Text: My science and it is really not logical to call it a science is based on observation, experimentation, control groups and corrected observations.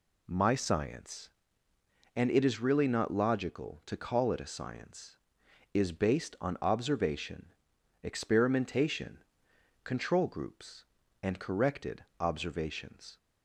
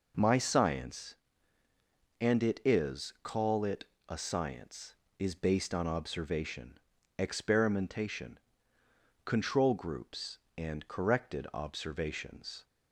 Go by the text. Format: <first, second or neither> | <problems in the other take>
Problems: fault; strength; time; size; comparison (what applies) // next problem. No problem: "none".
first | skips "really not logical to"; at 3.1 s // pauses between "it" and "a"; slight; at 3.8 s; 0.24 s long